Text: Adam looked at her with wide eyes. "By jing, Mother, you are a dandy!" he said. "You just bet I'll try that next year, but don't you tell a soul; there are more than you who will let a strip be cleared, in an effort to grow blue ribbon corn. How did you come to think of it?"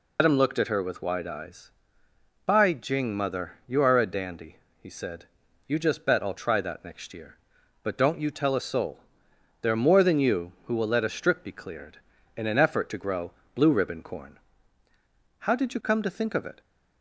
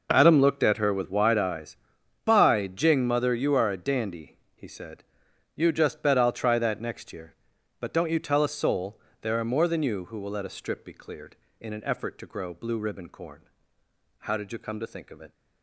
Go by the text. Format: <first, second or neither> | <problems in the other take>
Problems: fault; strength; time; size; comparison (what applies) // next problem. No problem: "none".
second | loses the start of "Adam"; at 0.1 s; 130 ms // pauses between "grow" and "blue"; slight; at 13.3 s; 0.24 s long